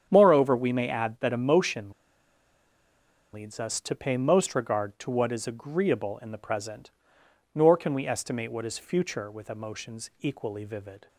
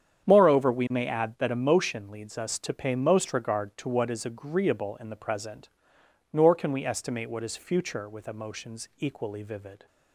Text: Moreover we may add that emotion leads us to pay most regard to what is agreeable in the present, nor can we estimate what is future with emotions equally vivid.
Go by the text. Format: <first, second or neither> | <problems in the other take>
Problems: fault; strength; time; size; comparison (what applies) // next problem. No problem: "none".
second | starts louder than the rest; strong; until 1.1 s; 8.5 dB; strong in the second // pauses between "emotion" and "leads"; strong; at 1.9 s; 1.4 s long